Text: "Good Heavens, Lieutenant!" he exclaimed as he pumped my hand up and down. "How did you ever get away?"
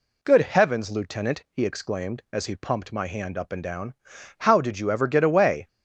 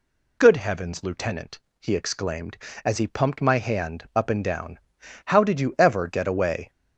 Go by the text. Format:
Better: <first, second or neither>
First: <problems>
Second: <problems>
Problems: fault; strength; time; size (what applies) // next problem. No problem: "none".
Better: neither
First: none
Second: none